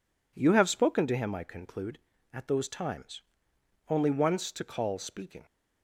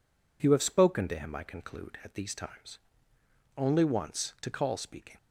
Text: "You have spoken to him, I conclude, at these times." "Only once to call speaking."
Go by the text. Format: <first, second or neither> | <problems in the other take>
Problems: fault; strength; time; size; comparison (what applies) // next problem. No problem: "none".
second | says "those" for "these"; at 2.4 s